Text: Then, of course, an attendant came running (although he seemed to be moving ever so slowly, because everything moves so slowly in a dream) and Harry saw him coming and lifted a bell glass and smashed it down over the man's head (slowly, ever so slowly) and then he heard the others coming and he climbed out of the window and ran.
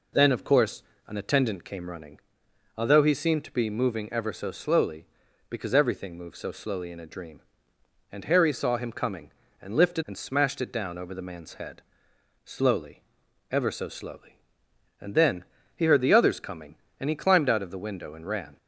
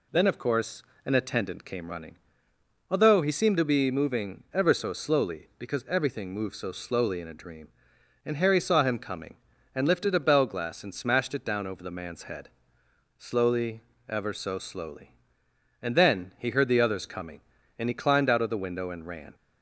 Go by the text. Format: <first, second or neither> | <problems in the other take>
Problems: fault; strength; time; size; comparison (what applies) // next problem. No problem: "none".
second | skips "a bell glass"; at 10.0 s // pauses between "then" and "he"; slight; at 15.4 s; 0.28 s long